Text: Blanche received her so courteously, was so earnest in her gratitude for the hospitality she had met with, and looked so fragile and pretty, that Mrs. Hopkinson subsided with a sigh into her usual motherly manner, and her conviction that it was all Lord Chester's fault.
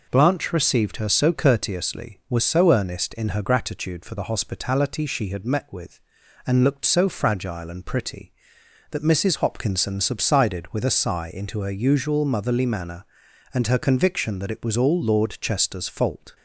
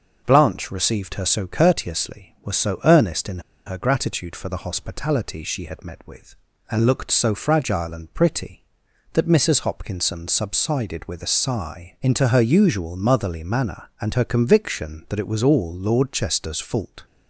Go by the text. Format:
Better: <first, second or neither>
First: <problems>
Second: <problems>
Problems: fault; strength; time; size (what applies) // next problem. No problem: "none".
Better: first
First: none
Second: pauses between "in" and "her"; slight; at 3.3 s; 0.26 s long